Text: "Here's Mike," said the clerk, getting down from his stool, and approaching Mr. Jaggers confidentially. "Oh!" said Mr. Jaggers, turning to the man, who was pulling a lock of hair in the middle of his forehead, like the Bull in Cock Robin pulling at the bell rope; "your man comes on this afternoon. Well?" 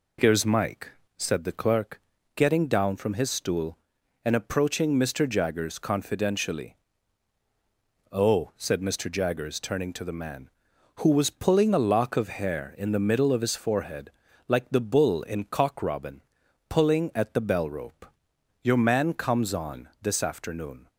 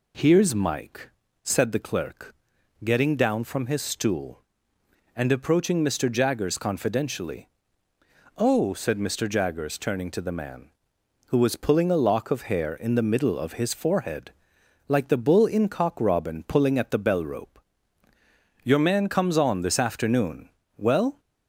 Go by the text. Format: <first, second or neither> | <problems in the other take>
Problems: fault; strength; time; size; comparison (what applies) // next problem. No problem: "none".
second | pauses between "Robin" and "pulling"; noticeable; at 16.2 s; 0.46 s long // stops before "Well"; at 20.8 s